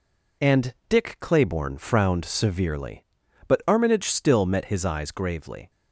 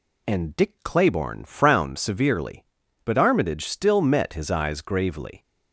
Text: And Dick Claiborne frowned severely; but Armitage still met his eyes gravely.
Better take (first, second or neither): neither